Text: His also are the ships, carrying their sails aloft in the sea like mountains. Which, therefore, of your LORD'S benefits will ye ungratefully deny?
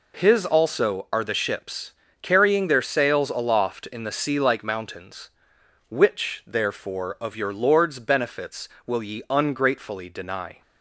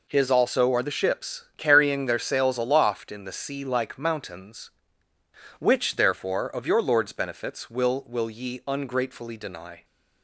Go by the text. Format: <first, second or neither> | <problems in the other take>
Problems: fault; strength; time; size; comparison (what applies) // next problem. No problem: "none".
first | says "will" twice; at 8.0 s